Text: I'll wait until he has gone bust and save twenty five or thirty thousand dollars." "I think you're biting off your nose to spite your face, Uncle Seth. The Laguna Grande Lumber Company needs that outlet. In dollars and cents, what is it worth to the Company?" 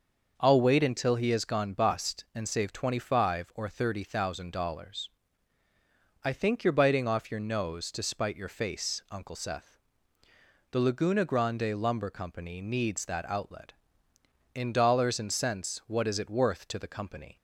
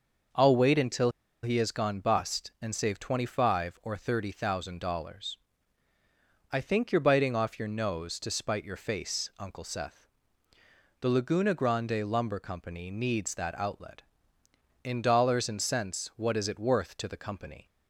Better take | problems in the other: first | starts louder than the rest; noticeable; until 1.6 s; 6 dB; noticeable in the first // pauses between "until" and "he"; slight; at 1.1 s; 0.32 s long

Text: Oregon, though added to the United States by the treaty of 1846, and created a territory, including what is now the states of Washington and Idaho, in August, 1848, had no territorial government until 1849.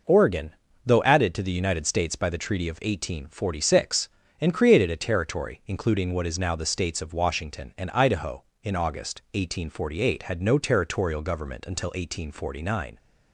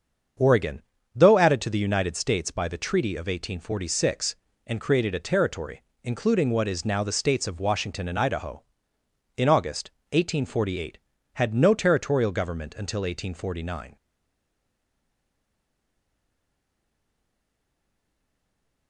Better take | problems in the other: first | starts louder than the rest; until 1.7 s; 7 dB // stays silent after the last word; strong; from 13.9 s on; 4.9 s long

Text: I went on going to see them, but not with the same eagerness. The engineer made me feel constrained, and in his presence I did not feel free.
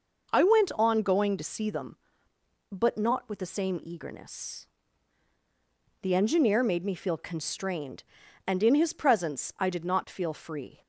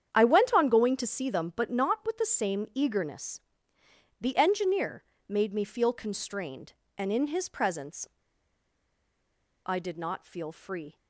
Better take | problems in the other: first | starts louder than the rest; strong; until 1.1 s; 8.5 dB // pauses between "engineer" and "made"; slight; at 5.0 s; 0.24 s long // pauses between "presence" and "I"; strong; at 8.0 s; 1.5 s long

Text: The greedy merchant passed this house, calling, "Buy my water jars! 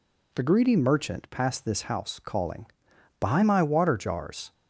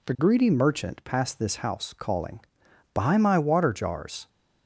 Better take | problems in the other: neither | none

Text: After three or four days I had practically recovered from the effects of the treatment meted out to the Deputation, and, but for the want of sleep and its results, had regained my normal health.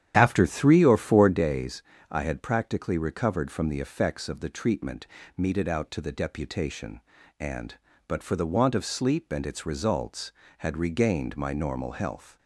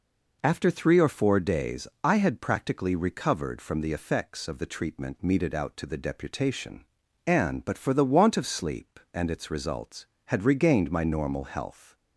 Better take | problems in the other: second | starts louder than the rest; strong; until 1.4 s; 10 dB // pauses between "days" and "I"; slight; at 1.8 s; 0.28 s long; slight in the second // pauses between "treatment" and "meted"; slight; at 5.0 s; 0.30 s long

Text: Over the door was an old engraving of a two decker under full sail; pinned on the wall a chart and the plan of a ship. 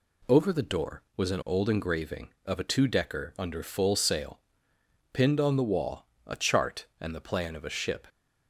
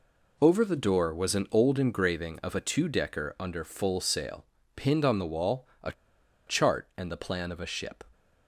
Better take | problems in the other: first | pauses between "wall" and "a"; slight; at 5.6 s; 0.16 s long; slight in the first // pauses between "a" and "chart"; noticeable; at 5.9 s; 0.55 s long

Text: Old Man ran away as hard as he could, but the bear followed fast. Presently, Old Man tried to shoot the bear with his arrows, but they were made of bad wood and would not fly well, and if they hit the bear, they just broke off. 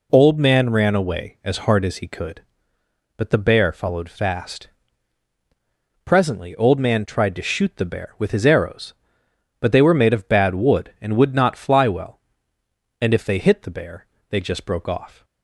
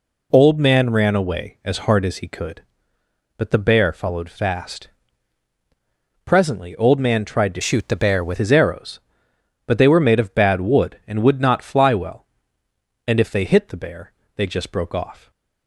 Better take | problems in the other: first | changes voice from "shoot" to "with"; from 7.6 to 8.3 s; 0.7 s long

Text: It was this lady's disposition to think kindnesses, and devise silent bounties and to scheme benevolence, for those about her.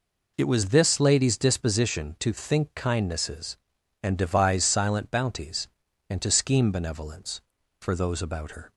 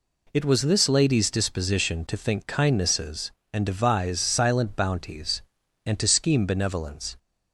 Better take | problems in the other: first | stops before "for those about her"; at 7.1 s

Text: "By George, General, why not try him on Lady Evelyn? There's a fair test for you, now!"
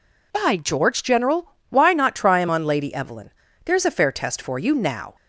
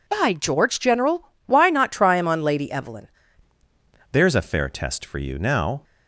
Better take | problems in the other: first | changes voice at "There's"; from 4.1 s on; 1.7 s long

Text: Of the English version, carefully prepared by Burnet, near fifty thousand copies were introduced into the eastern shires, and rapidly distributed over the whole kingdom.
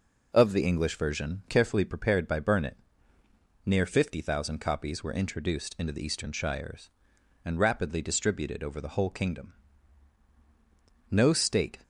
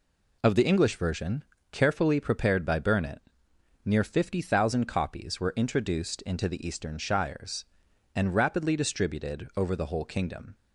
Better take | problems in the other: second | goes on to say "No state"; noticeable; from 11.1 s on; 0.72 s long

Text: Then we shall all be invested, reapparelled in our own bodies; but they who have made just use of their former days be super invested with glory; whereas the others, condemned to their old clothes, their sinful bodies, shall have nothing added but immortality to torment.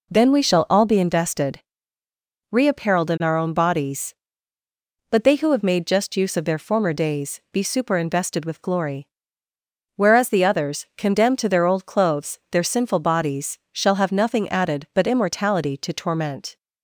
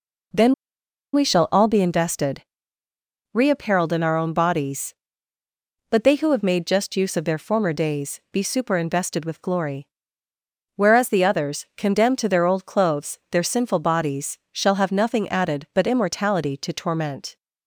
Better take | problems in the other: first | pauses between "Then" and "we"; noticeable; at 0.5 s; 0.60 s long

